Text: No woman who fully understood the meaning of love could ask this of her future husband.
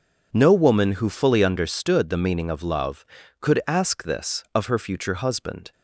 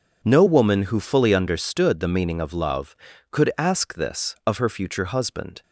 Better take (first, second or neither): neither